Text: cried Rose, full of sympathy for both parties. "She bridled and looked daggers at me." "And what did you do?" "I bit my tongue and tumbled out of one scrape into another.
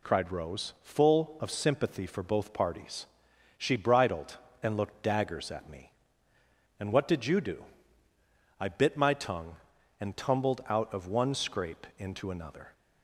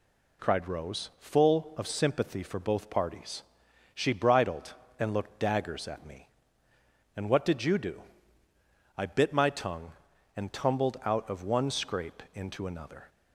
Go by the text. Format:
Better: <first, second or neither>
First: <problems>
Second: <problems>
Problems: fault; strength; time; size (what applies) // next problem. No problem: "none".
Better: neither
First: none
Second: none